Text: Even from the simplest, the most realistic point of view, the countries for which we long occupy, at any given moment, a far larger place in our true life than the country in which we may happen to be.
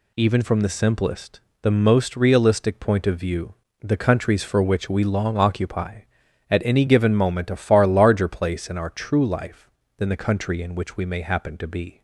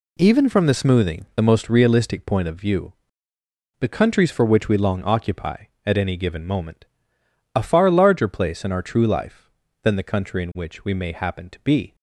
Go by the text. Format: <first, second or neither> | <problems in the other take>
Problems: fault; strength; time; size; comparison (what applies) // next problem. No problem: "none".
first | says "smoothing" for "simplest"; at 0.7 s